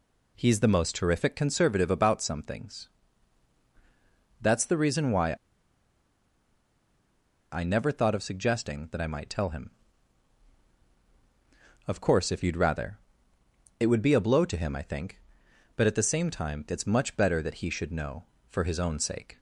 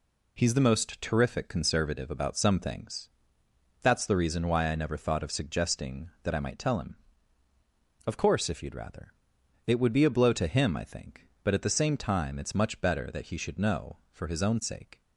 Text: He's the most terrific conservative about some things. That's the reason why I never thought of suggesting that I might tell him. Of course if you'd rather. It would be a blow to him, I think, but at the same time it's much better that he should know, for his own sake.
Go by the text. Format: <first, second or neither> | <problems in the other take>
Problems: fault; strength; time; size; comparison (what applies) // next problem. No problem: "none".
second | pauses between "why" and "I"; strong; at 5.3 s; 2.2 s long